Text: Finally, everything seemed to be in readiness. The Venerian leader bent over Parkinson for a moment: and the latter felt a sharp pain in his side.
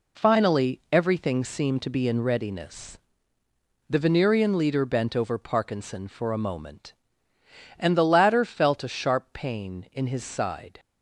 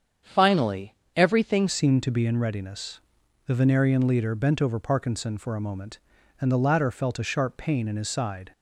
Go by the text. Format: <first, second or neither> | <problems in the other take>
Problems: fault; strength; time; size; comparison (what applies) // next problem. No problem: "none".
first | starts louder than the rest; strong; until 1.4 s; 7.5 dB // changes voice at "seemed"; from 1.6 s on; 6.9 s long